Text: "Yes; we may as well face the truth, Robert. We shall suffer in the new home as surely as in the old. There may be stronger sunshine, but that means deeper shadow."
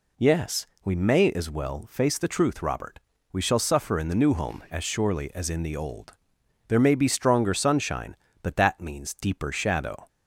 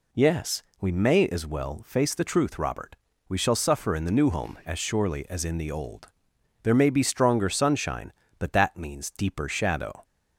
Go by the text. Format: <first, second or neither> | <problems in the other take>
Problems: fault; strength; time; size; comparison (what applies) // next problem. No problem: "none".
neither | none